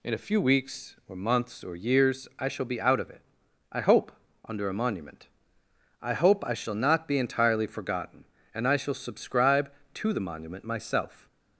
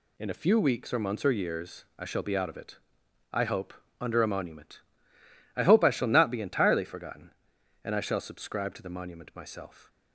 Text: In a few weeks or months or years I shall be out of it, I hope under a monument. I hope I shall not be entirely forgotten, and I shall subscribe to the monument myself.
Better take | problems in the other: neither | pauses between "hope" and "under"; slight; the same in both

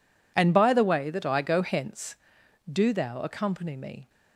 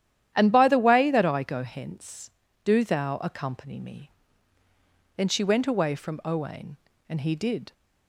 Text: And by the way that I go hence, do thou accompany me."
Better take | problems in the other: first | starts louder than the rest; strong; until 1.3 s; 11 dB // goes on to say "Then she went away from Owain and he did"; strong; from 5.1 s on; 2.5 s long

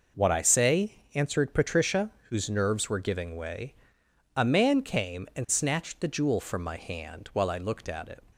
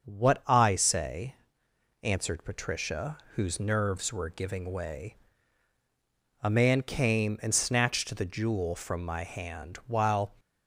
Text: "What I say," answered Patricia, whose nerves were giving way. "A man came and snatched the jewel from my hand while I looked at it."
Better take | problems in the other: first | starts louder than the rest; until 1.0 s; 6.5 dB // stops before "I looked at it"; at 10.3 s

